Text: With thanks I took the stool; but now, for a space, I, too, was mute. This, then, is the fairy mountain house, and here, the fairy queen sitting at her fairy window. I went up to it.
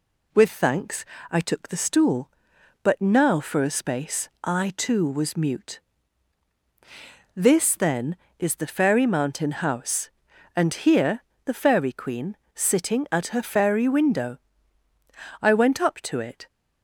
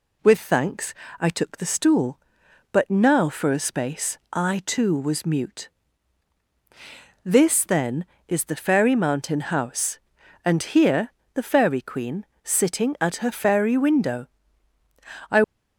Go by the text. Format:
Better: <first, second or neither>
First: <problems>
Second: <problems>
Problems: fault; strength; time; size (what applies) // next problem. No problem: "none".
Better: first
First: pauses between "thanks" and "I"; slight; at 1.0 s; 0.26 s long // pauses between "queen" and "sitting"; slight; at 12.3 s; 0.18 s long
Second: pauses between "thanks" and "I"; slight; at 0.9 s; 0.26 s long // pauses between "queen" and "sitting"; slight; at 12.2 s; 0.18 s long // stops before "went up to it"; at 15.4 s